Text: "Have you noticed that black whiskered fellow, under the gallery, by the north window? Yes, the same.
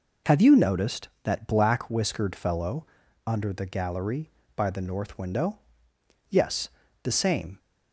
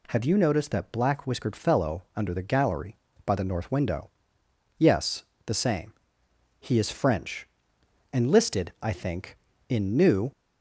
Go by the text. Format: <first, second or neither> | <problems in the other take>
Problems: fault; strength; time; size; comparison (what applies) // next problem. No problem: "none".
first | goes on to say "He is French enlisted I think in New"; strong; from 6.5 s on; 3.7 s long